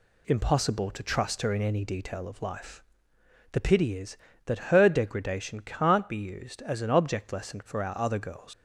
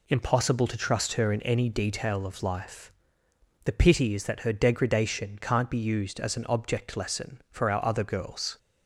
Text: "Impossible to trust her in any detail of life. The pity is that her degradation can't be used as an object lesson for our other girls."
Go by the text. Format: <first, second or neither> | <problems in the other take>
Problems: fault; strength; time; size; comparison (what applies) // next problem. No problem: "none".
second | leaves "girls" unfinished; at 8.5 s; 115 ms